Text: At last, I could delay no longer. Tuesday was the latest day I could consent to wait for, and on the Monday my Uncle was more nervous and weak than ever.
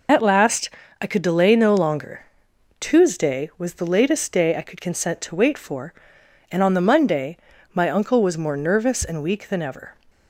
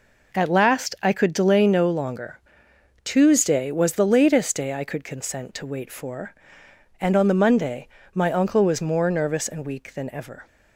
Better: second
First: loses the start of "At"; at 0.0 s; 55 ms // pauses between "Monday" and "my"; slight; at 7.3 s; 0.36 s long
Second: pauses between "Monday" and "my"; slight; at 7.8 s; 0.26 s long

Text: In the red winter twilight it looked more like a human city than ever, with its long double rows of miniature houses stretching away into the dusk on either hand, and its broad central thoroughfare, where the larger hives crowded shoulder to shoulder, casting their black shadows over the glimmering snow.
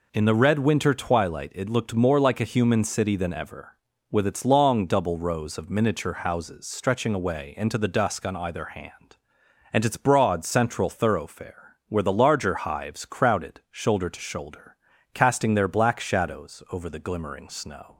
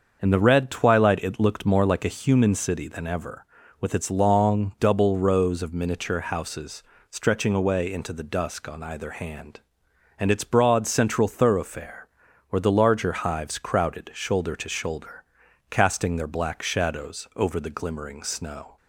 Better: first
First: none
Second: starts louder than the rest; until 1.2 s; 6.5 dB // skips "winter"; at 0.7 s // pauses between "houses" and "stretching"; slight; at 6.8 s; 0.28 s long

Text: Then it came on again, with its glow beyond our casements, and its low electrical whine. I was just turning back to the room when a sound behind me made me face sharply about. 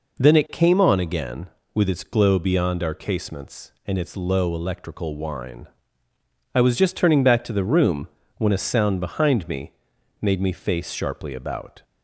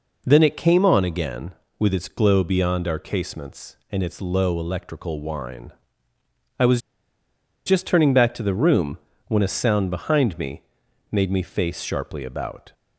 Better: first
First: pauses between "room" and "when"; slight; at 8.0 s; 0.28 s long // pauses between "me" and "made"; noticeable; at 9.7 s; 0.50 s long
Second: pauses between "was" and "just"; noticeable; at 6.7 s; 0.86 s long // pauses between "room" and "when"; slight; at 8.9 s; 0.28 s long // pauses between "me" and "made"; noticeable; at 10.6 s; 0.50 s long

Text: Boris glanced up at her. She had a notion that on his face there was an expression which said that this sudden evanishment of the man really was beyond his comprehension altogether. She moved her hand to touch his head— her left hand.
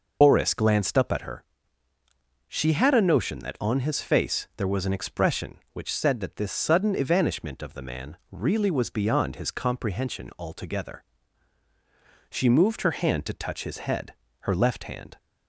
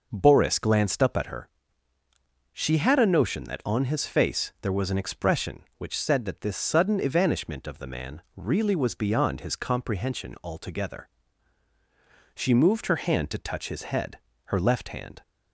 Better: second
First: loses the start of "Boris"; at 0.2 s; 135 ms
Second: none

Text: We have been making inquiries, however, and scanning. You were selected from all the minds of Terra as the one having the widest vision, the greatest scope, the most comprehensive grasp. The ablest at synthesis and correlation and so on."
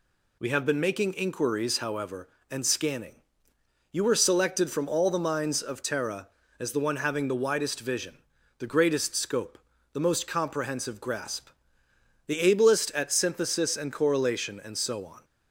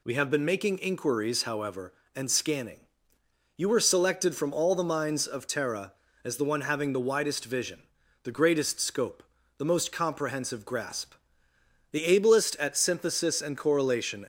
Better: first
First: none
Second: stops before "and so on"; at 14.2 s

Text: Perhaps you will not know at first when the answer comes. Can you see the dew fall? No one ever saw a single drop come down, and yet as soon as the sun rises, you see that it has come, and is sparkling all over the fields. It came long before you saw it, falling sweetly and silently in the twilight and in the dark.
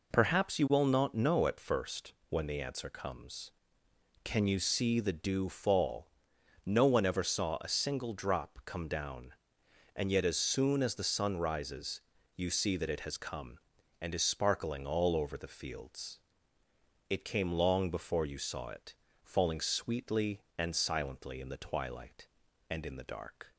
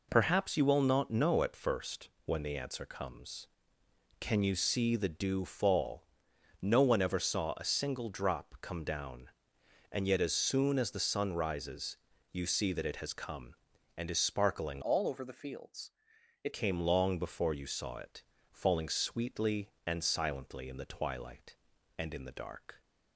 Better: first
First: pauses between "first" and "when"; slight; at 2.1 s; 0.16 s long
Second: pauses between "first" and "when"; slight; at 2.0 s; 0.16 s long // changes voice from "all" to "It"; from 14.8 to 16.5 s; 1.7 s long

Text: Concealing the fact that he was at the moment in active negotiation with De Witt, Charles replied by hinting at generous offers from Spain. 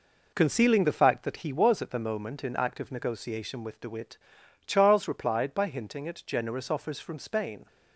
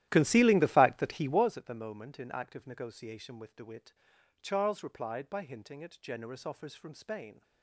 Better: first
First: none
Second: starts louder than the rest; strong; until 1.5 s; 13.5 dB

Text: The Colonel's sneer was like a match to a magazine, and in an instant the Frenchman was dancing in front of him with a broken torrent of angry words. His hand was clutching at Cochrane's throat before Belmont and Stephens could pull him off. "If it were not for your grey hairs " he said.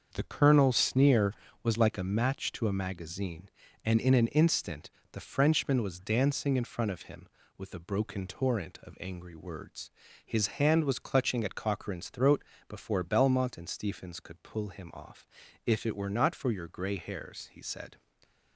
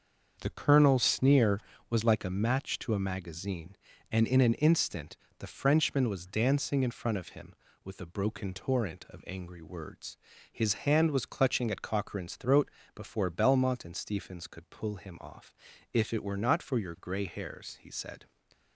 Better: neither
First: starts louder than the rest; until 1.1 s; 6.5 dB // pauses between "instant" and "the"; slight; at 4.8 s; 0.22 s long // pauses between "throat" and "before"; slight; at 12.4 s; 0.24 s long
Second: starts louder than the rest; until 1.4 s; 6.5 dB // pauses between "instant" and "the"; slight; at 5.1 s; 0.22 s long // pauses between "throat" and "before"; slight; at 12.7 s; 0.24 s long

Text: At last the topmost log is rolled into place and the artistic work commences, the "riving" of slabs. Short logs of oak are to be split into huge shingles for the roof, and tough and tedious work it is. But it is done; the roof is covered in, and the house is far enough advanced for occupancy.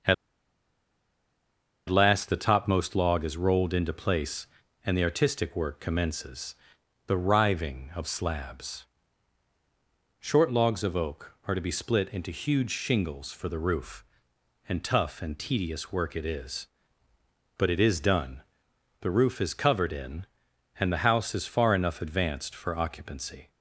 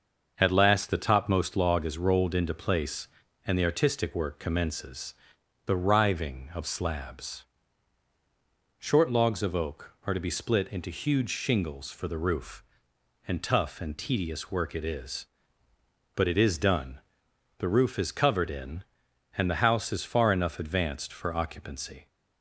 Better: second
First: starts louder than the rest; until 2.8 s; 6.5 dB // pauses between "At" and "last"; strong; at 0.1 s; 1.7 s long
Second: starts louder than the rest; until 1.3 s; 6.5 dB

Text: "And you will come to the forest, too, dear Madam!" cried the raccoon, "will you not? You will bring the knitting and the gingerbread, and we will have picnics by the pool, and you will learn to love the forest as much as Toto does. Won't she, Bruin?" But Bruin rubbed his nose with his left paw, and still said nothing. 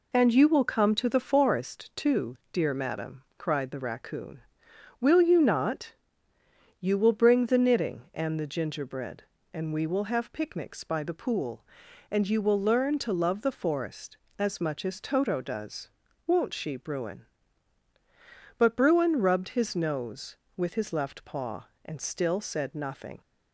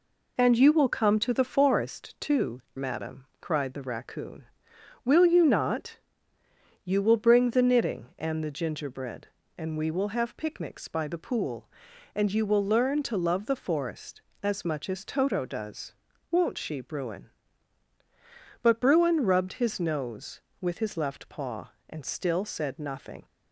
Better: first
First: none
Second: skips "dear"; at 2.6 s

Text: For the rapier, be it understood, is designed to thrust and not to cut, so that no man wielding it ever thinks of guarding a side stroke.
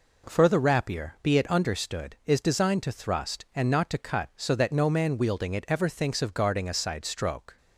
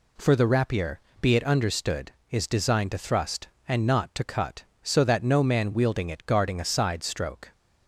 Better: first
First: none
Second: skips "ever thinks of"; at 6.2 s

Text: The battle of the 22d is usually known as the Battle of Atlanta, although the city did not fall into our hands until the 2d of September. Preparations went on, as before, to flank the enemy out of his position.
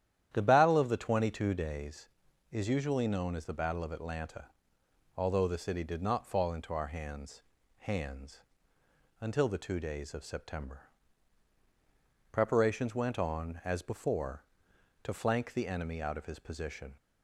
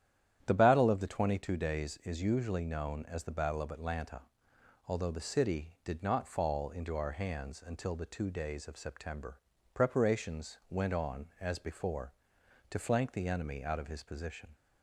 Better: second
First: starts louder than the rest; strong; until 1.3 s; 10.5 dB // says "hands" twice; at 7.7 s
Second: starts louder than the rest; strong; until 1.4 s; 10.5 dB

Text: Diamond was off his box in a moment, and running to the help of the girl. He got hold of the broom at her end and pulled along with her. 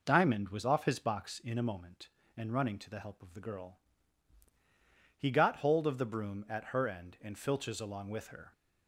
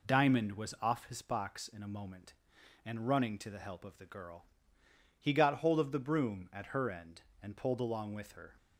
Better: second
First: says "filches" for "pulled"; at 7.3 s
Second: none

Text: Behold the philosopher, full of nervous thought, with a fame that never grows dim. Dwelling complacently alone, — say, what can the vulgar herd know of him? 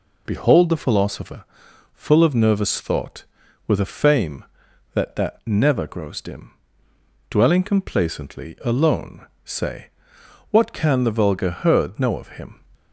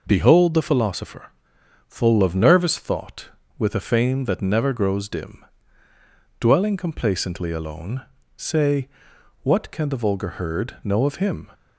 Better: second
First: says "that" twice; at 5.1 s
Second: none

